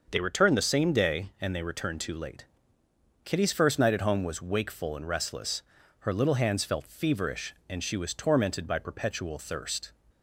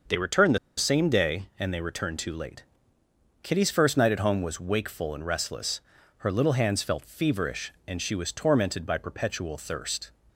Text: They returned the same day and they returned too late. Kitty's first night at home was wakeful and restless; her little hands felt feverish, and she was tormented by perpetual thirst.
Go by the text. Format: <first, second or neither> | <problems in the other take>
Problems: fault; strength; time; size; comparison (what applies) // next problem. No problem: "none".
first | starts louder than the rest; until 1.3 s; 6.5 dB; also in the first // pauses between "the" and "same"; slight; at 0.5 s; 0.21 s long